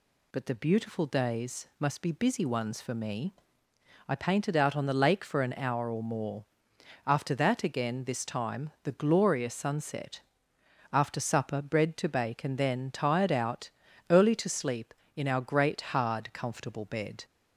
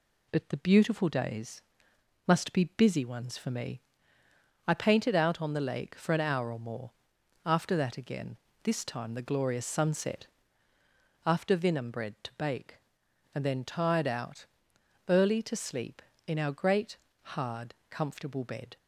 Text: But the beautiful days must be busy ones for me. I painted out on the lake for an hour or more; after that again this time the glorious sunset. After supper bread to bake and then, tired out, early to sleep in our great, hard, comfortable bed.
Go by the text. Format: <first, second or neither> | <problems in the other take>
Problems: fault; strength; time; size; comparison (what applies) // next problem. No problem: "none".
first | pauses between "days" and "must"; noticeable; at 1.6 s; 0.64 s long // pauses between "again" and "this"; slight; at 8.3 s; 0.28 s long // says "vinum" for "supper"; at 11.5 s